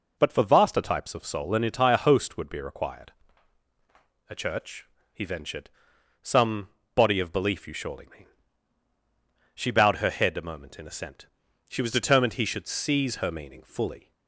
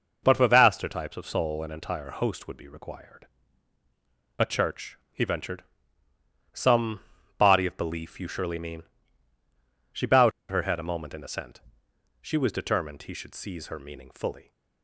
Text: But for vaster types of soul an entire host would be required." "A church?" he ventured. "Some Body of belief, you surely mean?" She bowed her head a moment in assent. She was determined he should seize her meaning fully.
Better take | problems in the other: first | pauses between "Some" and "Body"; slight; at 7.0 s; 0.36 s long; slight in the first // pauses between "bowed" and "her"; slight; at 10.3 s; 0.20 s long

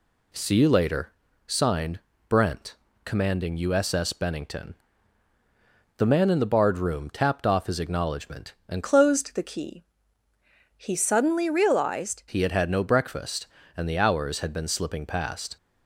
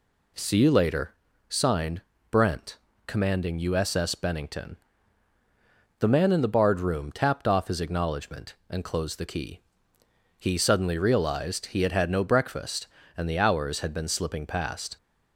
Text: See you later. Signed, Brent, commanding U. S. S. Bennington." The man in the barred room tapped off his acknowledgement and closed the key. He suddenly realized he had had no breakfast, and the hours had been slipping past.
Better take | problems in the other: second | changes voice from "closed" to "realized"; from 8.8 to 12.2 s; 3.4 s long

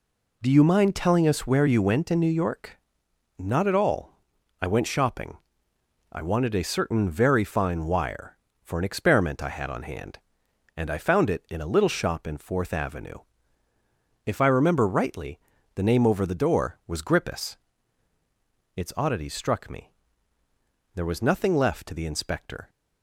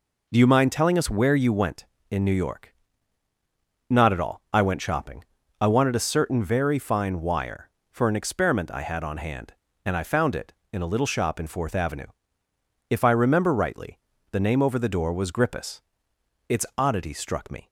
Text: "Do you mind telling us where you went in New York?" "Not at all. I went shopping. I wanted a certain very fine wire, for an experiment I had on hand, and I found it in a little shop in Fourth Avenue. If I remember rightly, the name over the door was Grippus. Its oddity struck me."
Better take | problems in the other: second | goes on to say "There was nothing left to the Inspector"; strong; from 20.9 s on; 1.7 s long

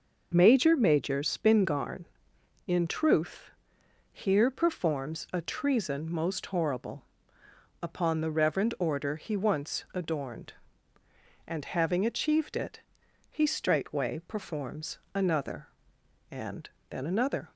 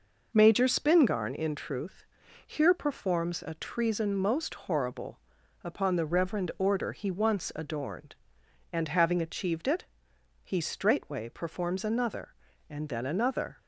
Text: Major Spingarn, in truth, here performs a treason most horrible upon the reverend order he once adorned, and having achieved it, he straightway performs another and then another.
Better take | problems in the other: second | says "Major" twice; at 0.7 s // pauses between "horrible" and "upon"; noticeable; at 7.0 s; 0.80 s long; also in the second // pauses between "performs" and "another"; slight; at 14.9 s; 0.18 s long // pauses between "and" and "then"; slight; at 16.7 s; 0.18 s long

